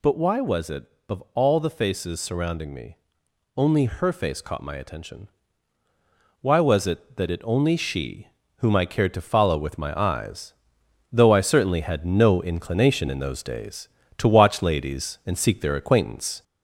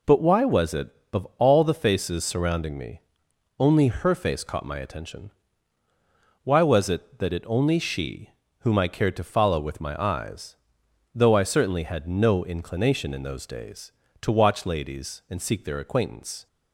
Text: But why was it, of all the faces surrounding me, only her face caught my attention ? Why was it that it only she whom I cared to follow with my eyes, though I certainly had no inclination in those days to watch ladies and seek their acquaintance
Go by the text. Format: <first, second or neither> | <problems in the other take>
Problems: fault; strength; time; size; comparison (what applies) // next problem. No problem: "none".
second | gets louder; slight; throughout; 3 dB // pauses between "she" and "whom"; slight; at 8.2 s; 0.28 s long; slight in the second